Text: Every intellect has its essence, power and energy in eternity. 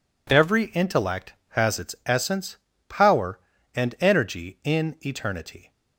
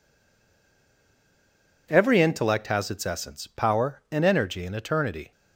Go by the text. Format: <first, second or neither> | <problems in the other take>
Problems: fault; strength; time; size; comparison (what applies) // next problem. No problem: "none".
first | stays silent before the first word; noticeable; until 1.8 s; 1.8 s long